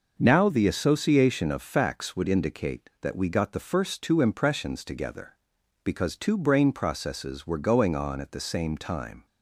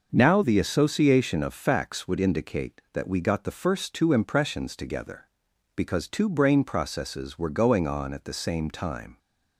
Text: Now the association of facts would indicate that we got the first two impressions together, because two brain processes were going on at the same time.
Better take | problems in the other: neither | none

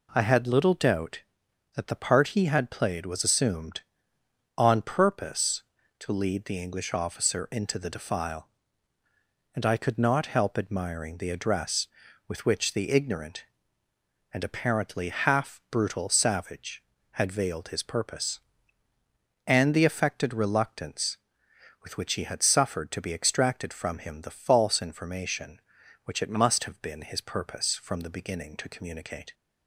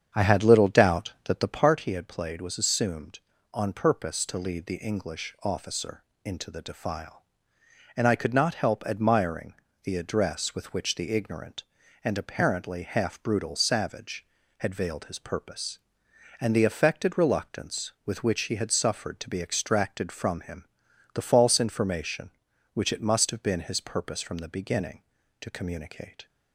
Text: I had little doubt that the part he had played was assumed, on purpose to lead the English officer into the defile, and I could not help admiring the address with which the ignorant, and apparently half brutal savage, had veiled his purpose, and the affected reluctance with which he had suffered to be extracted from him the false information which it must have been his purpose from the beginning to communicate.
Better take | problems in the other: first | starts louder than the rest; strong; until 1.7 s; 8 dB // pauses between "officer" and "into"; slight; at 6.0 s; 0.22 s long // pauses between "admiring" and "the"; slight; at 9.5 s; 0.30 s long // pauses between "him" and "the"; noticeable; at 20.6 s; 0.48 s long

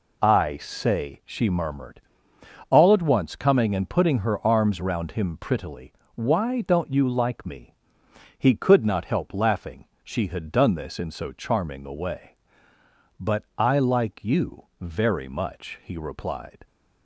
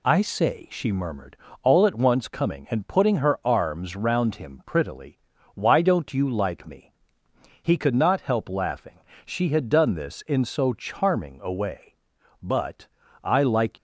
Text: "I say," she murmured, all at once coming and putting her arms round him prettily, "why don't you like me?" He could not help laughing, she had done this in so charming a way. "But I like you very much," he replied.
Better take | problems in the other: first | pauses between "But" and "I"; at 12.8 s; 0.38 s long // stops before "you very much he replied"; at 13.7 s

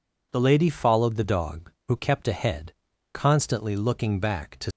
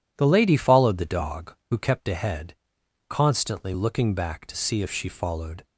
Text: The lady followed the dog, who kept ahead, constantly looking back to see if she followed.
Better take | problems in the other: second | stops before "see if she followed"; at 4.7 s

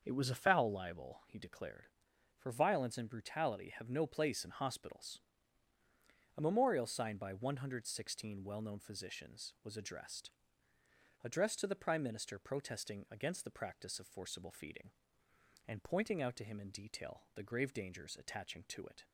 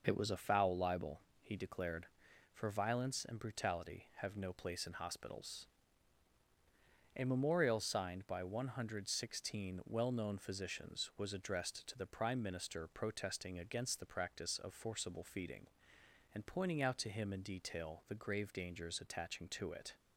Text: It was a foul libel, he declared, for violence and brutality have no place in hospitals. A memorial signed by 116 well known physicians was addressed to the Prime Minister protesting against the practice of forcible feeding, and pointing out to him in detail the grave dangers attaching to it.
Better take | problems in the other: second | starts louder than the rest; until 1.0 s; 6.5 dB // says "addressed" twice; at 11.2 s

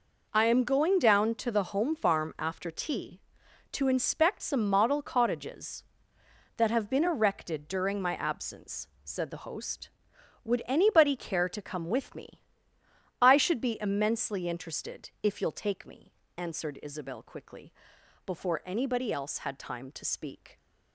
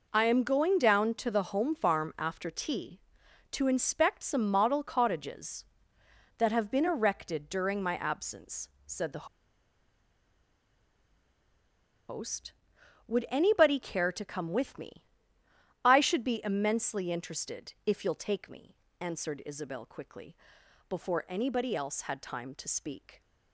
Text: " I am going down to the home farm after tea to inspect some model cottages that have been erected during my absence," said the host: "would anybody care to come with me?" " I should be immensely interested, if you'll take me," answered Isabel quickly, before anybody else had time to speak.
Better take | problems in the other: first | pauses between "the" and "host"; strong; at 9.2 s; 2.8 s long

